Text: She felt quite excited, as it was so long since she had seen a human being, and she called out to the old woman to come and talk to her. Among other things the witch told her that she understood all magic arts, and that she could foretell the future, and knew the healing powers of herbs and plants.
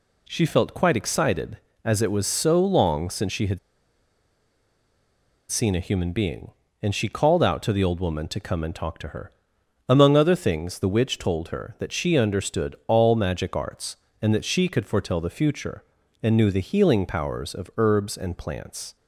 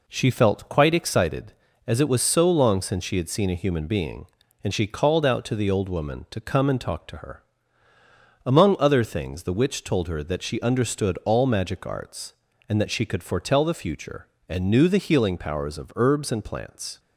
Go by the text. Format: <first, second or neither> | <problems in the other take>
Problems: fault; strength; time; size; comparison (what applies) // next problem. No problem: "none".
second | pauses between "had" and "seen"; strong; at 3.5 s; 1.9 s long